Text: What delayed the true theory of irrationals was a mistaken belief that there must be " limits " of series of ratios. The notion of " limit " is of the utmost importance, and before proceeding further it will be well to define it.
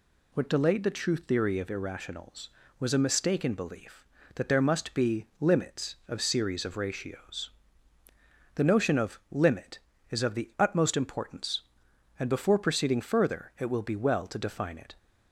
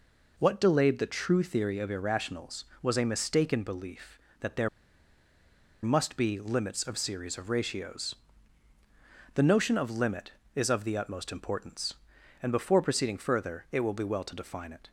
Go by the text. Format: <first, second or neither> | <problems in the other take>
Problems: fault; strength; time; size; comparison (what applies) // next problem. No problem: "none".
first | pauses between "there" and "must"; at 4.6 s; 1.1 s long